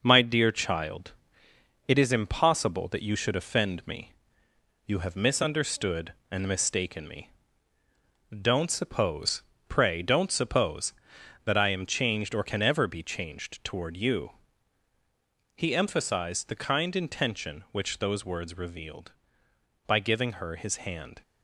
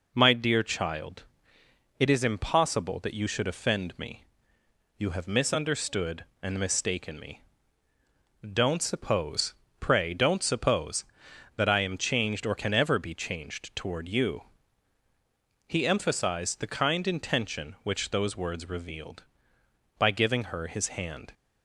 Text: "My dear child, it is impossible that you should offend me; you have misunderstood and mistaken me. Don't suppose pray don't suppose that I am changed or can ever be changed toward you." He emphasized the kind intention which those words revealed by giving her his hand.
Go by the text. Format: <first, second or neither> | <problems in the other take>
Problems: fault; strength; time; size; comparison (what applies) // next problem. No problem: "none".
second | gets quieter; noticeable; throughout; 5 dB // pauses between "suppose" and "pray"; slight; at 9.4 s; 0.26 s long; slight in the second